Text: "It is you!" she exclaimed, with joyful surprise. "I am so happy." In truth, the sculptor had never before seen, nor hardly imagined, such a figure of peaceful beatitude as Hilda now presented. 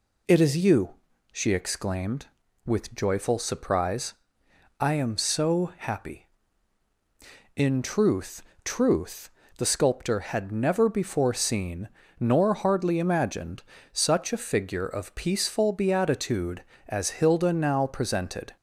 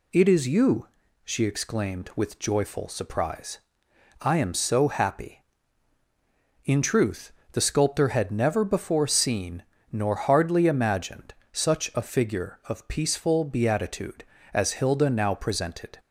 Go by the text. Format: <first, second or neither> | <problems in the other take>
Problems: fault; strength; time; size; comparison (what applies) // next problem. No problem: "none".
second | says "truth" twice; at 8.6 s